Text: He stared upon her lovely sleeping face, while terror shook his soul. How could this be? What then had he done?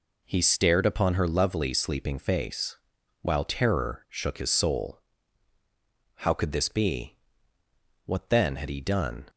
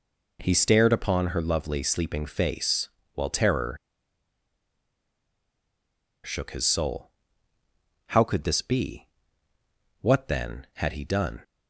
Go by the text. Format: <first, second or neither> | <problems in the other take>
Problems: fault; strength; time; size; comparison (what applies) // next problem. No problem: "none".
first | pauses between "terror" and "shook"; strong; at 3.7 s; 2.4 s long